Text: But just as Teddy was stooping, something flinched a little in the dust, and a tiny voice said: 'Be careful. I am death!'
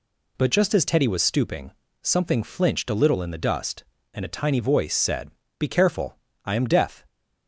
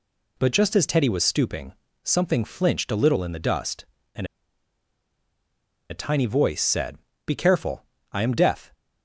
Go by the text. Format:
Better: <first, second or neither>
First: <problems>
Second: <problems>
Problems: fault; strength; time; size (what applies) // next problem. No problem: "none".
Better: first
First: none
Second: pauses between "and" and "a"; strong; at 4.2 s; 1.6 s long